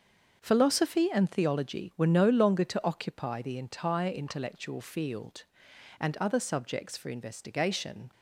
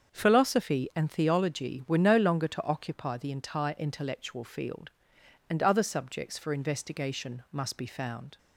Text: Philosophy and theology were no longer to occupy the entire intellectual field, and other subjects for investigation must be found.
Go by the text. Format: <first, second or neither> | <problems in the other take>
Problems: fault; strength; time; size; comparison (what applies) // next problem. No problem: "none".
second | starts louder than the rest; until 1.4 s; 6.5 dB; also in the second // stops before "must be found"; at 8.1 s